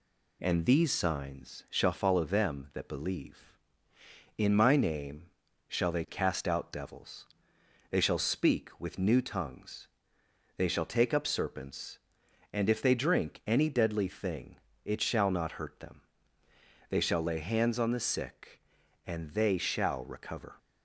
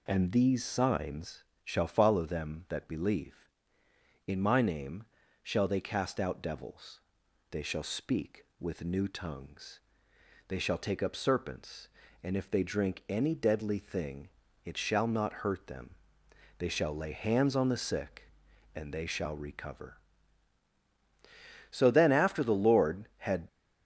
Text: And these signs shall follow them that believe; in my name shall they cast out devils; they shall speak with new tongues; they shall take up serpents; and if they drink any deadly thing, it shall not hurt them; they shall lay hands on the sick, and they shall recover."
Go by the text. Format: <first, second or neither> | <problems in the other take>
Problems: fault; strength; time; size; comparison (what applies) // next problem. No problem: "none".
first | pauses between "signs" and "shall"; slight; at 1.4 s; 0.22 s long // pauses between "name" and "shall"; at 5.0 s; 0.40 s long; also in the first // goes on to say "So then after the Lord had"; strong; from 21.7 s on; 1.7 s long